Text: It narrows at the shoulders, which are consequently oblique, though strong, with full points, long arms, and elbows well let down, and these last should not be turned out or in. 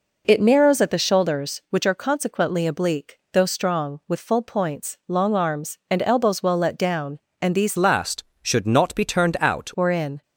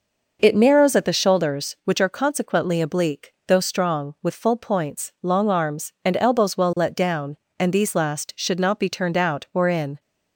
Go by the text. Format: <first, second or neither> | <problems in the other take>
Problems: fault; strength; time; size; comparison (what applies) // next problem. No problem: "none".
second | changes voice from "last" to "out"; from 7.7 to 9.7 s; 2.0 s long